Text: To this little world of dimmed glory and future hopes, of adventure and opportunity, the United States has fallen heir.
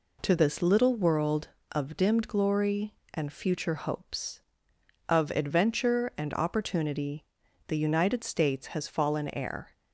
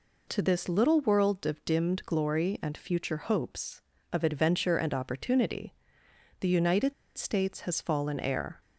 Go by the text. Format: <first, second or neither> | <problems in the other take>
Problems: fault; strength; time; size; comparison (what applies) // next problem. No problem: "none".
first | pauses between "United" and "States"; slight; at 6.9 s; 0.24 s long